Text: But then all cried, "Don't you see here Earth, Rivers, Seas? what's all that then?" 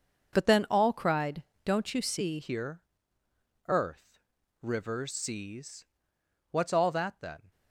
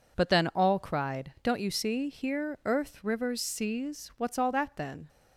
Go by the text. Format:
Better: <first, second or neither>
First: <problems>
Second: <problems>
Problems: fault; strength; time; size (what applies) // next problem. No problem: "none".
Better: second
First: starts louder than the rest; until 1.3 s; 6.5 dB // changes voice at "here"; from 2.4 s on; 5.1 s long // pauses between "here" and "Earth"; noticeable; at 2.8 s; 0.84 s long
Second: none